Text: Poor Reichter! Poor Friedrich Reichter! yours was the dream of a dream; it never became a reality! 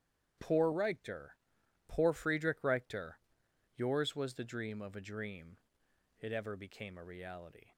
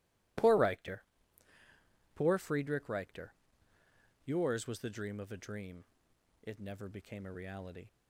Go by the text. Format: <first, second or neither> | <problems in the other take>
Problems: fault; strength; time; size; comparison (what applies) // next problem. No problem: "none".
second | starts louder than the rest; strong; until 1.9 s; 9.5 dB // says "ever" for "never"; at 6.3 s